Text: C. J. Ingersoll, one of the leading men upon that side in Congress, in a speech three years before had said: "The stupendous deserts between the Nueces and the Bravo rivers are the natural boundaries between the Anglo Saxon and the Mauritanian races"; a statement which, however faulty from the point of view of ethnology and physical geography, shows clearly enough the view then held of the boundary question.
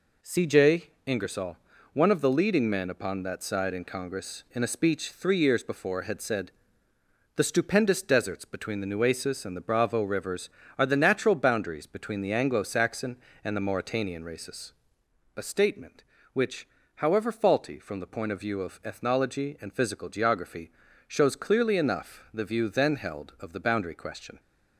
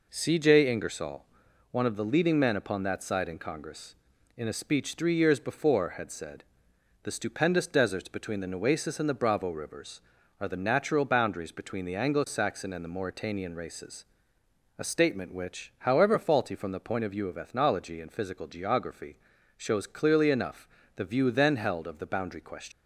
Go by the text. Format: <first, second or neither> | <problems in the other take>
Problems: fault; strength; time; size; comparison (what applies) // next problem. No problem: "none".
first | pauses between "enough" and "the"; slight; at 20.6 s; 0.30 s long // leaves "question" unfinished; at 22.7 s; 105 ms